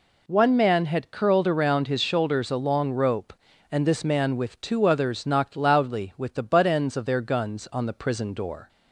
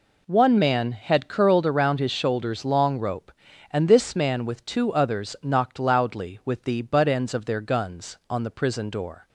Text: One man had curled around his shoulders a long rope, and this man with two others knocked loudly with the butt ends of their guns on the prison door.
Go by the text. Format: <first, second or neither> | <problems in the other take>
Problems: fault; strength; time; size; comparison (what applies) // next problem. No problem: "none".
first | skips "a"; at 2.6 s